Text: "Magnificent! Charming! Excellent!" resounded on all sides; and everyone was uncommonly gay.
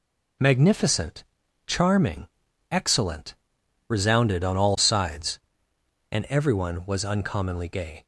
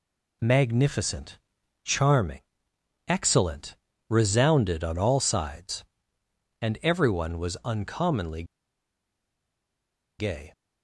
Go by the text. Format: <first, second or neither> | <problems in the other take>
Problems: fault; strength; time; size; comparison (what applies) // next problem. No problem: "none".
first | pauses between "uncommonly" and "gay"; strong; at 8.4 s; 1.7 s long